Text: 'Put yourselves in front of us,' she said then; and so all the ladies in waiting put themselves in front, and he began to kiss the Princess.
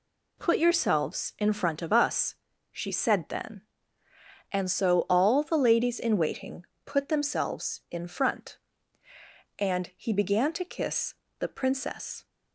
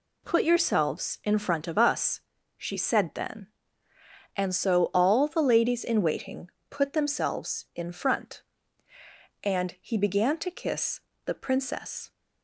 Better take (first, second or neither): neither